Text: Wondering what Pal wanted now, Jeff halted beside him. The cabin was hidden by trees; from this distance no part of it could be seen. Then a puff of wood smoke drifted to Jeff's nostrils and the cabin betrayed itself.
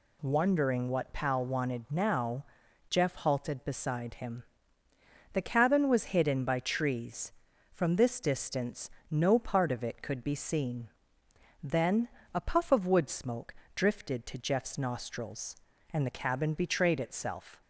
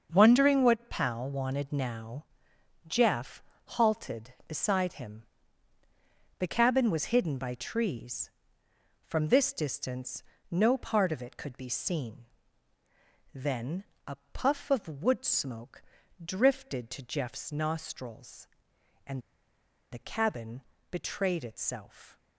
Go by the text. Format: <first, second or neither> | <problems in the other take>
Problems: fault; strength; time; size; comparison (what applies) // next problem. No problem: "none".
first | starts louder than the rest; until 1.1 s; 6.5 dB // pauses between "Jeff" and "halted"; slight; at 3.4 s; 0.36 s long // pauses between "distance" and "no"; slight; at 10.2 s; 0.26 s long; slight in the first // pauses between "Then" and "a"; slight; at 13.8 s; 0.20 s long; slight in the first // pauses between "a" and "puff"; slight; at 14.1 s; 0.16 s long // pauses between "smoke" and "drifted"; at 15.8 s; 0.44 s long; slight in the first // pauses between "and" and "the"; noticeable; at 19.2 s; 0.71 s long // pauses between "cabin" and "betrayed"; slight; at 20.6 s; 0.28 s long